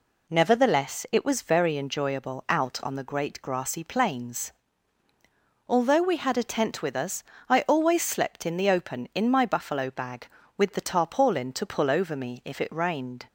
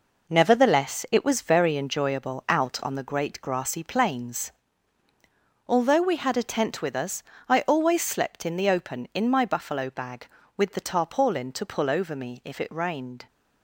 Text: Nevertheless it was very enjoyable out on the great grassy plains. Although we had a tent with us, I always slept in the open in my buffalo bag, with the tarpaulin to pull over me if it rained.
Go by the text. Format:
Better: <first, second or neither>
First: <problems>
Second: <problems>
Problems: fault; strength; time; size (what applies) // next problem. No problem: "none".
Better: first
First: none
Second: gets quieter; strong; throughout; 7.5 dB